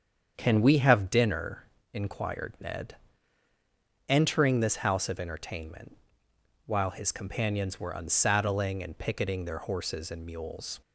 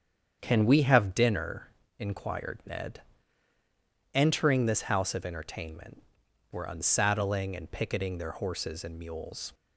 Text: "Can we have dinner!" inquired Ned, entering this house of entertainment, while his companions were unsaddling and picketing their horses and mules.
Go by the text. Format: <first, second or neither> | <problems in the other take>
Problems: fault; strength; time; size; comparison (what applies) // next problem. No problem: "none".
first | starts louder than the rest; strong; until 1.4 s; 7.5 dB; strong in the first // skips "while his companions"; at 6.2 s